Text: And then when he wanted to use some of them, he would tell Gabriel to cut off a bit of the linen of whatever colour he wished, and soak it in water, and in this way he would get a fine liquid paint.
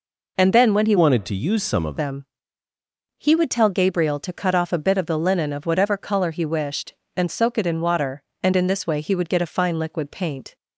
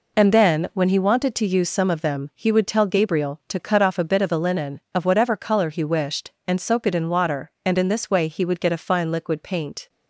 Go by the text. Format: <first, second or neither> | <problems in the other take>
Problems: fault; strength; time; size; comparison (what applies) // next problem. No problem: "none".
second | changes voice from "wanted" to "of"; from 0.9 to 1.9 s; 1.0 s long